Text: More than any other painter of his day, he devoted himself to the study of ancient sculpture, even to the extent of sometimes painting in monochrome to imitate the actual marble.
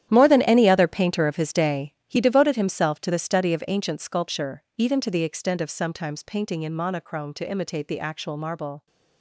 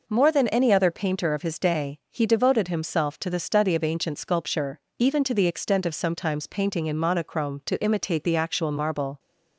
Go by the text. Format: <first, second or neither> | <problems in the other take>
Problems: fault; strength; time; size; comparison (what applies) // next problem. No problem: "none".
second | gets quieter; strong; throughout; 14 dB